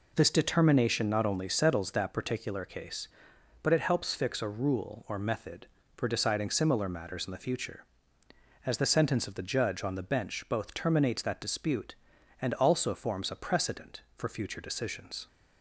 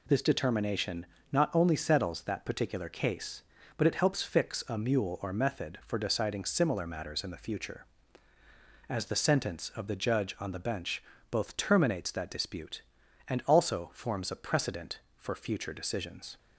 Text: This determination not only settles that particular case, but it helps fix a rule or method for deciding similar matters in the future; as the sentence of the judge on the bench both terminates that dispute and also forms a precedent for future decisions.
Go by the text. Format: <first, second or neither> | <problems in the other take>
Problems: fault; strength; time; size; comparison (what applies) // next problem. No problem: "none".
first | pauses between "determination" and "not"; slight; at 1.0 s; 0.26 s long // says "mule" for "rule"; at 4.7 s // pauses between "bench" and "both"; slight; at 11.0 s; 0.26 s long